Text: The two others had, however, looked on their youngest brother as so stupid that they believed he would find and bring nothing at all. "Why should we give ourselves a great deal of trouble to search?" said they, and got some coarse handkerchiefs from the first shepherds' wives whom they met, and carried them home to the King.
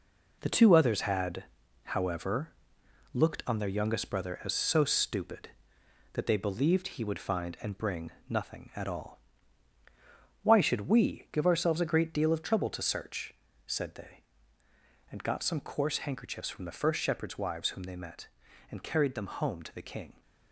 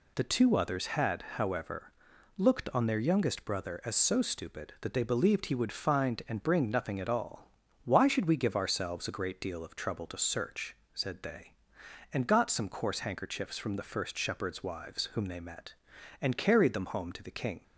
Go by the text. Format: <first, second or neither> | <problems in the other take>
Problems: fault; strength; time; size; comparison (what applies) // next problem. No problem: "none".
second | gets quieter; strong; throughout; 7 dB // pauses between "bring" and "nothing"; slight; at 8.1 s; 0.18 s long